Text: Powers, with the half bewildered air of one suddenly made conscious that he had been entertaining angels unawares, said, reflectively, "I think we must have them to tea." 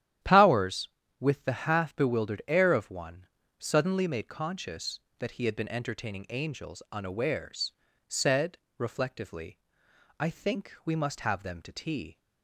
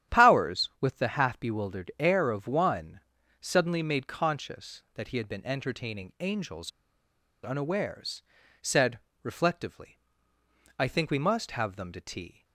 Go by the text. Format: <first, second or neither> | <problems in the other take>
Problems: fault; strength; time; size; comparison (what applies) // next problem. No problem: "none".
first | starts louder than the rest; strong; until 1.2 s; 10 dB; strong in the first // pauses between "one" and "suddenly"; at 2.9 s; 0.40 s long; slight in the first // pauses between "angels" and "unawares"; noticeable; at 6.7 s; 0.73 s long